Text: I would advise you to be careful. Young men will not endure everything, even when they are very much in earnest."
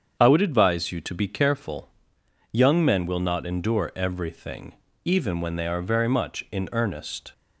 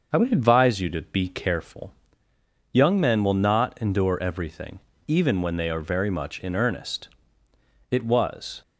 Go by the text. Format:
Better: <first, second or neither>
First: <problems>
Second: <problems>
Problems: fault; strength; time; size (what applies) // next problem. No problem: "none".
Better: first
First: starts louder than the rest; strong; until 1.2 s; 7.5 dB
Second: starts louder than the rest; until 1.1 s; 6 dB // goes on to say "It was"; noticeable; from 7.9 s on; 0.70 s long